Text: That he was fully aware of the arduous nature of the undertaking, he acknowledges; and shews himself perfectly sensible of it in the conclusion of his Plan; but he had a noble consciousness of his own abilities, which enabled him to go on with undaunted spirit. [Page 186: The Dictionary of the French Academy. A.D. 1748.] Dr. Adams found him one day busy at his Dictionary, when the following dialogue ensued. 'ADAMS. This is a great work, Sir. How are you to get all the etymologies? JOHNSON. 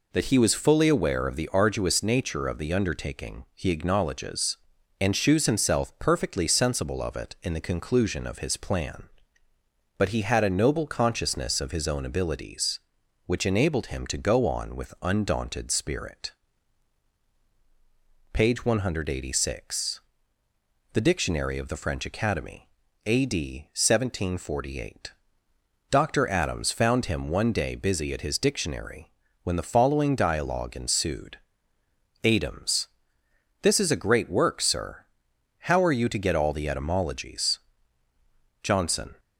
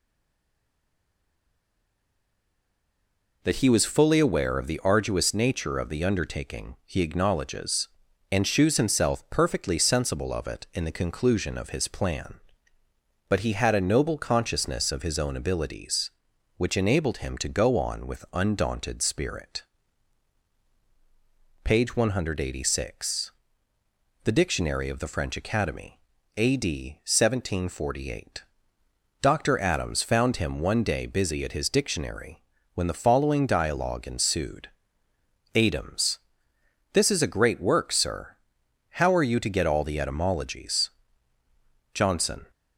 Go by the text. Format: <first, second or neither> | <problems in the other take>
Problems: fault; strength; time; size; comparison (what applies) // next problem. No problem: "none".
first | stays silent before the first word; strong; until 3.4 s; 3.4 s long